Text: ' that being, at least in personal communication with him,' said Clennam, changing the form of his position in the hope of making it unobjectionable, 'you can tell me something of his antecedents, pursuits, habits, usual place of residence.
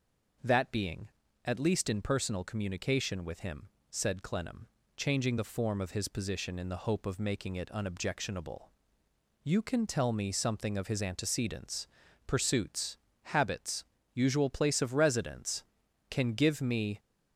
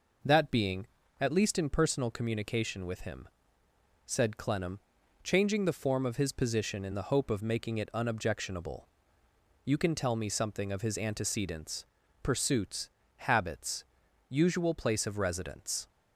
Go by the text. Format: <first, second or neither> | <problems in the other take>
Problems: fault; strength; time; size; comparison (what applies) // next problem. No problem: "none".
second | goes on to say "Can give me"; noticeable; from 16.0 s on; 0.90 s long